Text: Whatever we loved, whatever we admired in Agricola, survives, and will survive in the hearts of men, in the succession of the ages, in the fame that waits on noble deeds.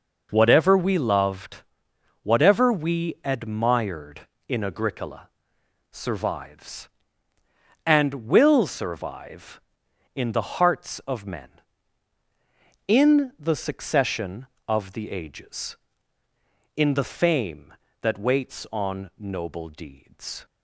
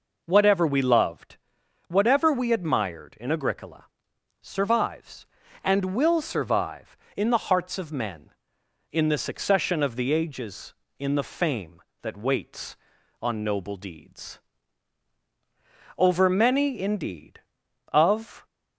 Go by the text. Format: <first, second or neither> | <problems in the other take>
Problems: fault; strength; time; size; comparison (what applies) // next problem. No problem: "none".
first | goes on to say "Over many indeed of"; strong; from 15.9 s on; 2.4 s long